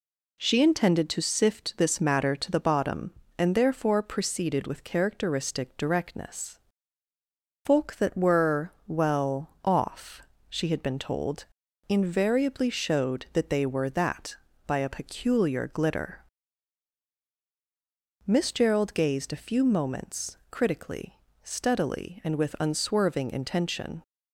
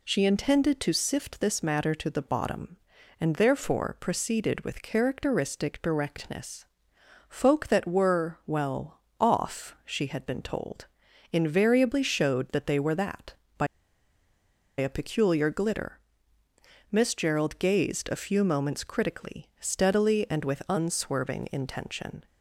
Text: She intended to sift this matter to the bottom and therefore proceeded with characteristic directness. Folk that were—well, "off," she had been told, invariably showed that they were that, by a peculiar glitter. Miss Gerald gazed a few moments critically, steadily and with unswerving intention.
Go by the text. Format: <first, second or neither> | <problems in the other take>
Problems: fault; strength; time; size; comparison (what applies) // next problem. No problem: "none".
first | pauses between "by" and "a"; at 13.6 s; 1.1 s long